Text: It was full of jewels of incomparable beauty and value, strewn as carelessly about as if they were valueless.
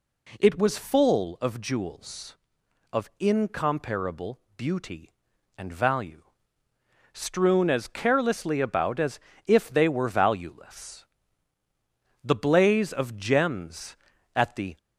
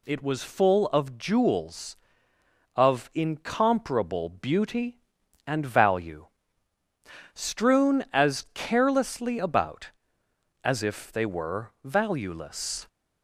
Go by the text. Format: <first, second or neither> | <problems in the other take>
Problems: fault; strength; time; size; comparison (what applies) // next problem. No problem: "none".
second | pauses between "incomparable" and "beauty"; slight; at 4.3 s; 0.16 s long // pauses between "as" and "if"; slight; at 9.1 s; 0.26 s long // goes on to say "The blaze of gems at the"; strong; from 12.2 s on; 2.5 s long